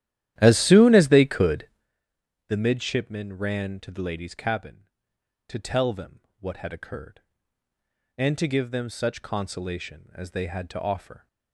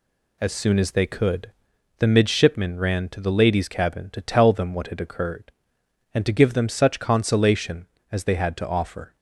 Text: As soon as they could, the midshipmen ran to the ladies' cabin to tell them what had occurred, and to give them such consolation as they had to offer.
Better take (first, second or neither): second